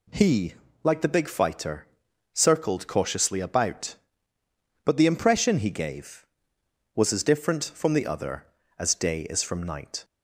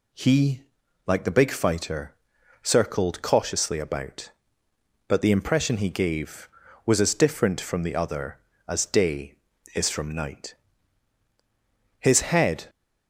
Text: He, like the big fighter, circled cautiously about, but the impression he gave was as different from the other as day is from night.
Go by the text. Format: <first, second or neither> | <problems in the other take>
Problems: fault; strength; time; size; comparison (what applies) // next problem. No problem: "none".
first | goes on to say "His head"; noticeable; from 11.9 s on; 0.68 s long